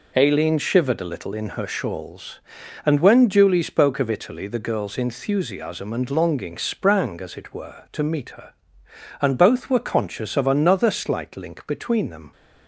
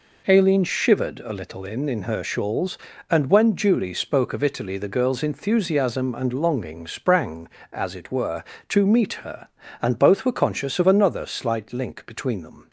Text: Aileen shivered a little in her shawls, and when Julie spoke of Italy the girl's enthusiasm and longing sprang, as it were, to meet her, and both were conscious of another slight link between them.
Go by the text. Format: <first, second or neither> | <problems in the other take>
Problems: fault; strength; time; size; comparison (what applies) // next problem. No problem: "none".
first | says "in" twice; at 1.8 s